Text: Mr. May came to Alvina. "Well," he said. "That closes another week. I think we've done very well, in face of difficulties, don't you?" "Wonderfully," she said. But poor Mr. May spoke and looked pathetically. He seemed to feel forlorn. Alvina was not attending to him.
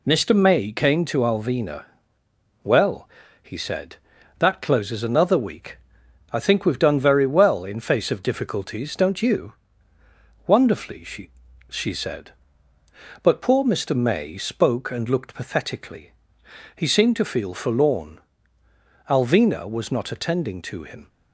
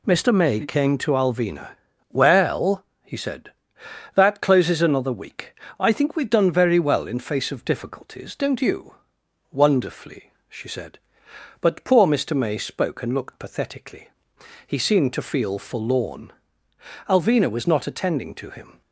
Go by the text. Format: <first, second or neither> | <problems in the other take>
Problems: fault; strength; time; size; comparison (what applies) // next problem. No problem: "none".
second | says "she" twice; at 11.6 s